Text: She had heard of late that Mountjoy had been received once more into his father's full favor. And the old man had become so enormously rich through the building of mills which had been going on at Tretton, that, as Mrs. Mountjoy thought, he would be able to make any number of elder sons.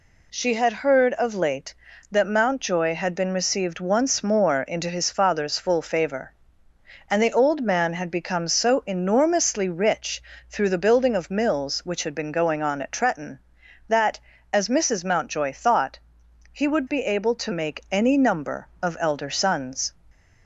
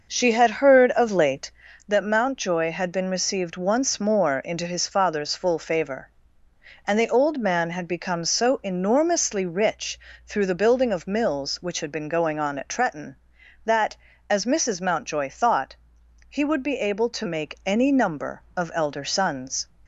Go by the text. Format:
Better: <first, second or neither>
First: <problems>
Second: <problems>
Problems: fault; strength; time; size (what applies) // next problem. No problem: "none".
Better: first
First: pauses between "rich" and "through"; slight; at 10.2 s; 0.26 s long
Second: starts louder than the rest; noticeable; until 1.7 s; 6 dB // pauses between "rich" and "through"; slight; at 9.9 s; 0.26 s long